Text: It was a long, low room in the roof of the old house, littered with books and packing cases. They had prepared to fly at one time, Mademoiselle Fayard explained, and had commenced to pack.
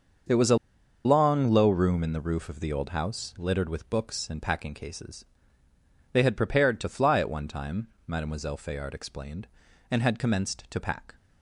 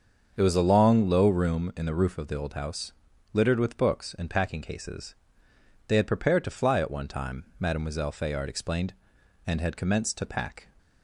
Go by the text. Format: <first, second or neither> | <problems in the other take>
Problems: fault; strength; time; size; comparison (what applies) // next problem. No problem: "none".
second | starts louder than the rest; until 1.7 s; 6.5 dB; also in the second // pauses between "a" and "long"; noticeable; at 0.5 s; 0.47 s long